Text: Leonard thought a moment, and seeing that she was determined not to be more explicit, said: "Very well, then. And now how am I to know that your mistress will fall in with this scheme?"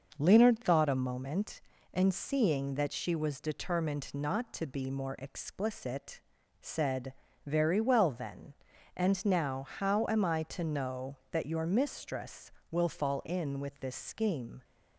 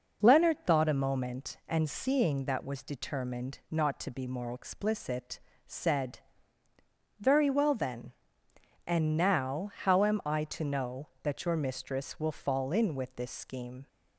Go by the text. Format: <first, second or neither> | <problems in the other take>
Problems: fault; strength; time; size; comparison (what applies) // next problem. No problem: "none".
first | skips "she"; at 2.6 s